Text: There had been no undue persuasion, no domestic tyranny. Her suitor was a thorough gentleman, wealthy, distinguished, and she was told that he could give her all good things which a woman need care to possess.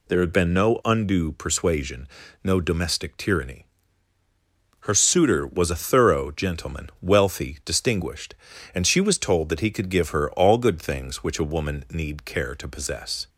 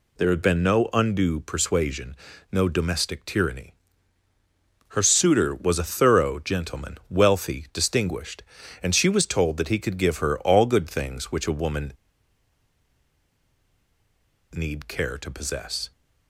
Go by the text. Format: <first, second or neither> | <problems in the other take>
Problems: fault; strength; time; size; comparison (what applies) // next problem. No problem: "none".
first | pauses between "woman" and "need"; strong; at 11.9 s; 2.6 s long